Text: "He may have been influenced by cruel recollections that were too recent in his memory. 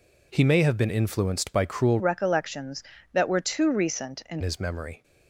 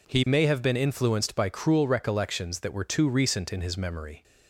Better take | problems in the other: second | changes voice from "recollections" to "in"; from 2.0 to 4.4 s; 2.4 s long

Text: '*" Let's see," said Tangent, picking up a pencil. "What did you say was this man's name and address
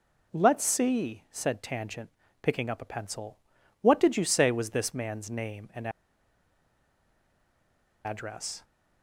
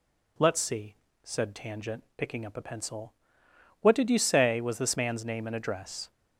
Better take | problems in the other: second | pauses between "and" and "address"; strong; at 5.8 s; 2.1 s long

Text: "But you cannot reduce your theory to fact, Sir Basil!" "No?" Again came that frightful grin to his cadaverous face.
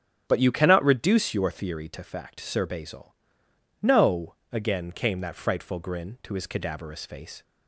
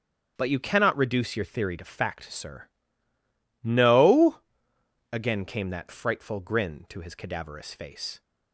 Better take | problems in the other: first | starts louder than the rest; strong; until 1.3 s; 8.5 dB; strong in the first // skips "Basil"; at 3.1 s

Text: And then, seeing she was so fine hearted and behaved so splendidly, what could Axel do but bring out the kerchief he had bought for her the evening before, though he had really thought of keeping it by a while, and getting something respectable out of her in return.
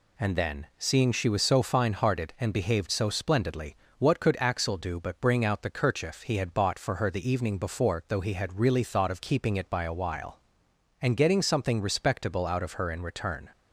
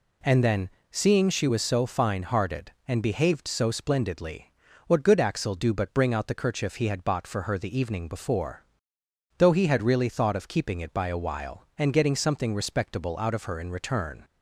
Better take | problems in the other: first | says "good" for "could"; at 5.0 s

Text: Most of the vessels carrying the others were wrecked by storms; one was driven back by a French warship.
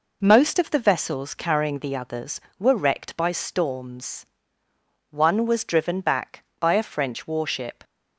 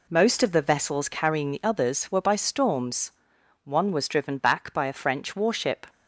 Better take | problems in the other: first | skips "wrecked"; at 2.2 s

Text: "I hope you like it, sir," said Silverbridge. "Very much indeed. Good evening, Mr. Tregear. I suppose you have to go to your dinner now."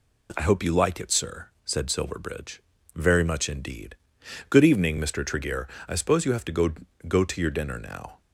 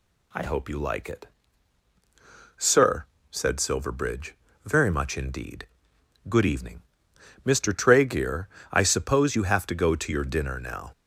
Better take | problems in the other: second | says "go" twice; at 7.0 s

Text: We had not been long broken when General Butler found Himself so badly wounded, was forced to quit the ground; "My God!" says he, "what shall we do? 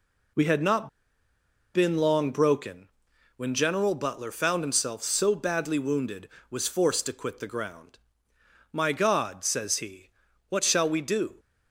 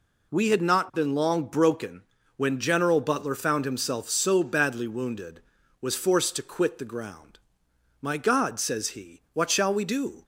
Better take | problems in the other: second | pauses between "not" and "been"; noticeable; at 0.8 s; 0.84 s long // pauses between "broken" and "when"; noticeable; at 2.8 s; 0.48 s long; slight in the second

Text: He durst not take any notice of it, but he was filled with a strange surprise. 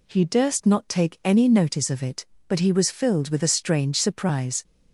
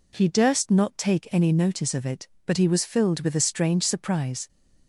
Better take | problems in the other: neither | none

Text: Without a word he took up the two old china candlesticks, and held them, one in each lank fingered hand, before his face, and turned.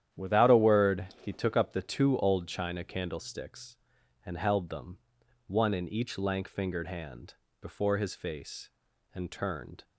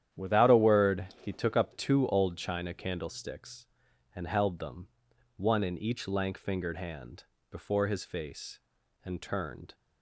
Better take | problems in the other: first | starts louder than the rest; strong; until 1.2 s; 10.5 dB; strong in the first // pauses between "word" and "he"; slight; at 1.0 s; 0.16 s long; slight in the first // skips "the"; at 1.7 s

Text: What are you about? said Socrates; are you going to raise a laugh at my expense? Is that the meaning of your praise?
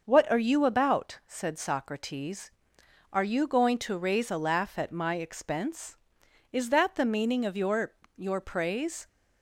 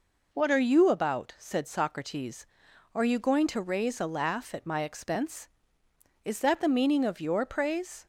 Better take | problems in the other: second | starts louder than the rest; until 1.0 s; 6 dB // says "your" twice; at 8.1 s

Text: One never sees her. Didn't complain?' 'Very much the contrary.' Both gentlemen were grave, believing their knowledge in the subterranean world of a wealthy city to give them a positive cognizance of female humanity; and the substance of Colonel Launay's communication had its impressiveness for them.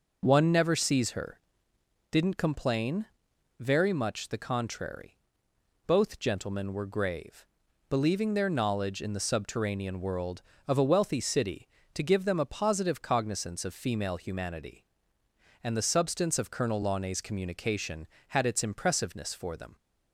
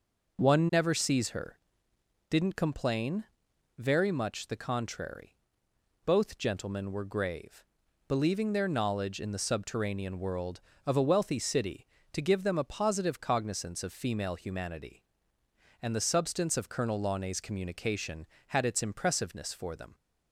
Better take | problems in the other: neither | none

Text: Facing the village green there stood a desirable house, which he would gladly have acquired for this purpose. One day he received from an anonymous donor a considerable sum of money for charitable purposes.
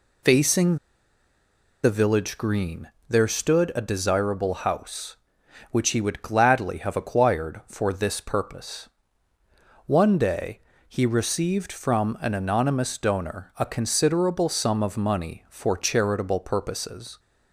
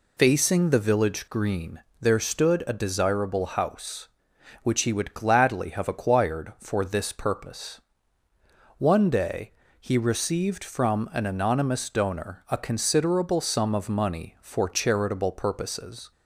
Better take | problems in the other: second | pauses between "Facing" and "the"; at 0.7 s; 1.0 s long // pauses between "green" and "there"; slight; at 2.8 s; 0.18 s long; slight in the second // pauses between "day" and "he"; slight; at 10.6 s; 0.26 s long; slight in the second

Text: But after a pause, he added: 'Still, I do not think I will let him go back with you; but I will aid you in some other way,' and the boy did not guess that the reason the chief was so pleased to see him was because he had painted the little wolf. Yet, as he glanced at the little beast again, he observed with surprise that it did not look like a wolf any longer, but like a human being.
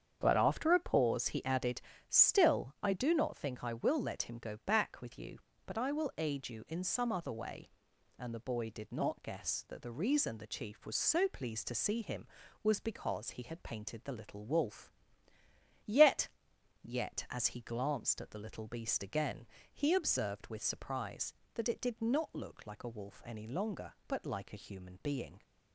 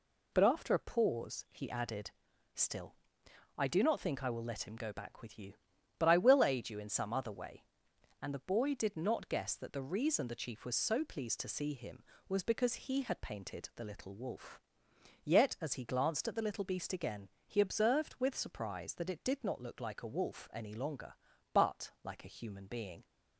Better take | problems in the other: second | starts louder than the rest; strong; until 1.2 s; 8 dB // says "Yet" twice; at 16.8 s

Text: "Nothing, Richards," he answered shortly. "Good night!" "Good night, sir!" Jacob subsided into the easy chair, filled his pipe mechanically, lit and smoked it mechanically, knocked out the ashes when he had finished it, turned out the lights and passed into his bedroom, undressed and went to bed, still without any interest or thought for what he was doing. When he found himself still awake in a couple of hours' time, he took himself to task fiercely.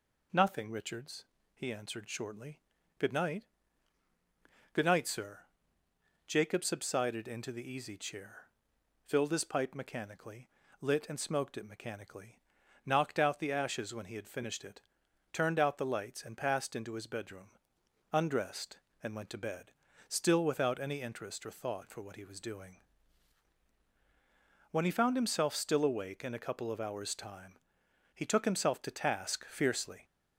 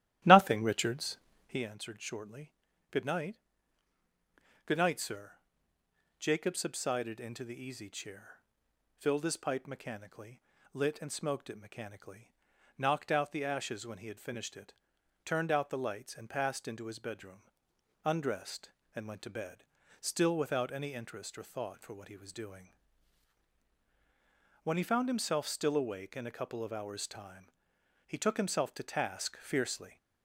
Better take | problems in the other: first | starts louder than the rest; strong; until 1.7 s; 13.5 dB

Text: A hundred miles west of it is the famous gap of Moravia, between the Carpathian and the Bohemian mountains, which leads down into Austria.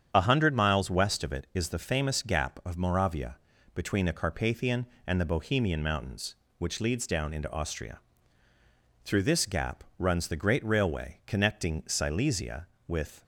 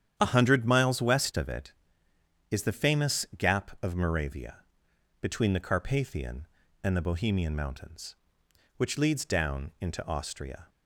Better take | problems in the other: second | starts louder than the rest; strong; until 1.1 s; 8 dB; strong in the second // goes on to say "Through this gap runs the great railway connecting Silesia with"; strong; from 9.0 s on; 4.1 s long

